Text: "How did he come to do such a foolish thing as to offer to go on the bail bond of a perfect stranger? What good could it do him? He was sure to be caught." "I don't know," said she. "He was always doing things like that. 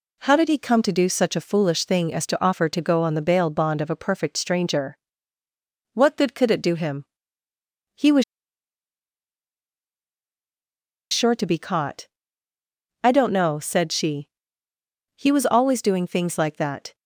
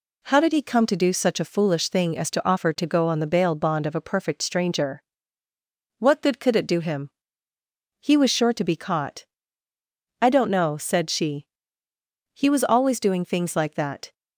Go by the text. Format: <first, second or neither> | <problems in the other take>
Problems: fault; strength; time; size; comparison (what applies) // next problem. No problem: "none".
second | pauses between "was" and "sure"; strong; at 8.2 s; 2.8 s long